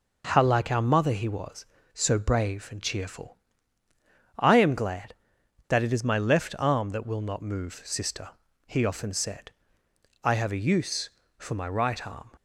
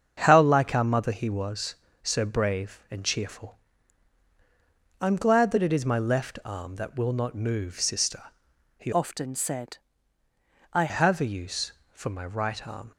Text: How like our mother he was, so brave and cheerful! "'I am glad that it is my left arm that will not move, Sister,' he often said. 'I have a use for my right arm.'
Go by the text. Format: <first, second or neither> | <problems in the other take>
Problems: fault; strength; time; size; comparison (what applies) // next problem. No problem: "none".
first | starts louder than the rest; strong; until 1.2 s; 7 dB // changes voice from "often" to "I"; from 8.9 to 10.8 s; 1.9 s long